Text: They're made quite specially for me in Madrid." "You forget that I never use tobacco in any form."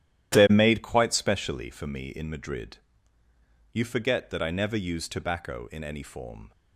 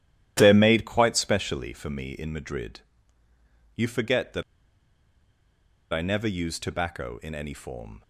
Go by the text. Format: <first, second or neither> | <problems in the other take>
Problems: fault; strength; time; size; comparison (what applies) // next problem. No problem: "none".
first | starts louder than the rest; strong; until 1.3 s; 12.5 dB; strong in the first // pauses between "that" and "I"; strong; at 4.4 s; 1.5 s long